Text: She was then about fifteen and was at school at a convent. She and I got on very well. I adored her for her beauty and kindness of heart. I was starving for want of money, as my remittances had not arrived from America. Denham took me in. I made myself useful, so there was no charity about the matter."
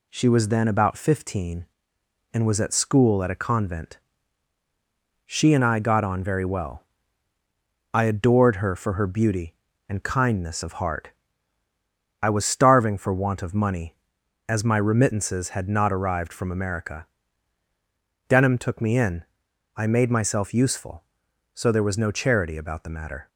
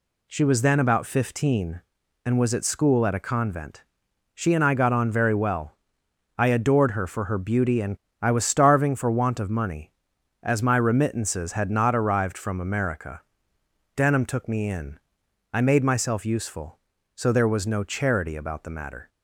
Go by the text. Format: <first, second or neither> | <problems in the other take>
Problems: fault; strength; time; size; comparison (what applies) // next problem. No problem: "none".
first | skips "kindness of heart"; at 8.0 s